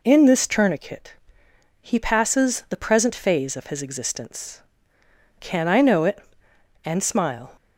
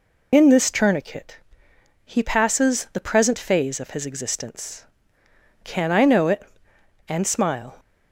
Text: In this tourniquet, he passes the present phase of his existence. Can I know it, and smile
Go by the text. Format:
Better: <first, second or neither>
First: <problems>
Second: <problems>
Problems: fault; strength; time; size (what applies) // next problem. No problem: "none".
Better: first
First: none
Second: loses the start of "In"; at 0.3 s; 55 ms